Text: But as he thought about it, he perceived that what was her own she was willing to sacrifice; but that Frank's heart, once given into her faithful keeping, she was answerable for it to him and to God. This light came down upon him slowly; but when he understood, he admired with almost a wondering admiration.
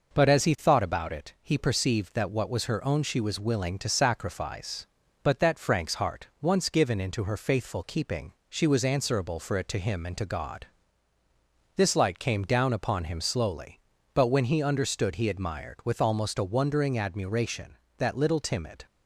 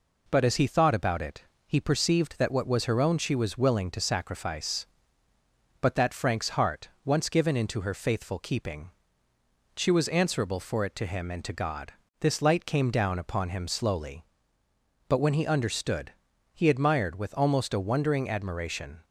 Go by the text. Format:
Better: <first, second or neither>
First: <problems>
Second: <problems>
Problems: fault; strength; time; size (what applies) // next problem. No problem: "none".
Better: second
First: goes on to say "That little timid"; noticeable; from 17.9 s on; 0.86 s long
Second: none